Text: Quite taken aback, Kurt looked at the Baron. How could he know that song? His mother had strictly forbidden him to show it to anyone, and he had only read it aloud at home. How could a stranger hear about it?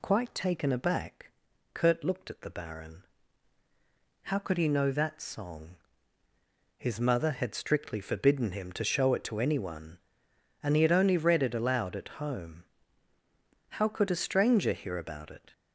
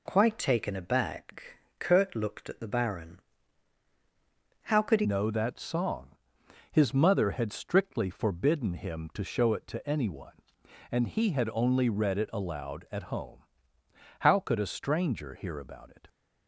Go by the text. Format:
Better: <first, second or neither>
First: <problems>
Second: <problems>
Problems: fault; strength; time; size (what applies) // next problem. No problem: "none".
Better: first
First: none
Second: changes voice at "know"; from 5.0 s on; 11.0 s long